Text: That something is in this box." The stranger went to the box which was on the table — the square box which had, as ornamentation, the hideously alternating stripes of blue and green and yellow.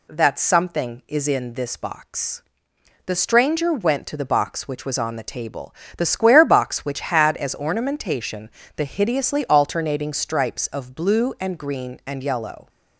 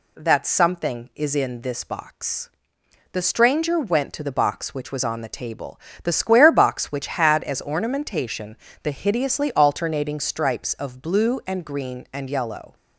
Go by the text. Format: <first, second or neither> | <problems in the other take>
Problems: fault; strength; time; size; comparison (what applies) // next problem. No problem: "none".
neither | none